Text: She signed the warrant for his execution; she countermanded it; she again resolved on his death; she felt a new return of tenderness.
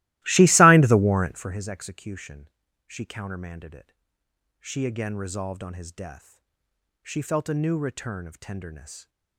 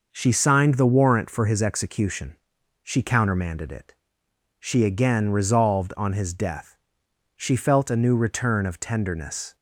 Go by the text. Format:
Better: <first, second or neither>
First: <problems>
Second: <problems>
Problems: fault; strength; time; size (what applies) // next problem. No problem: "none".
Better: second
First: starts louder than the rest; strong; until 1.6 s; 18 dB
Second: none